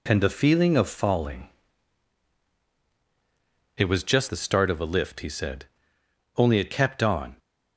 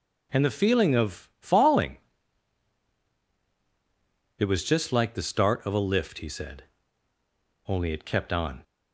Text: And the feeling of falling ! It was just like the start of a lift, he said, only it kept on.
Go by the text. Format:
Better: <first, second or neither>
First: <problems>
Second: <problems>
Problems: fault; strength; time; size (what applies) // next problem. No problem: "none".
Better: second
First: skips "like"; at 4.2 s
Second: none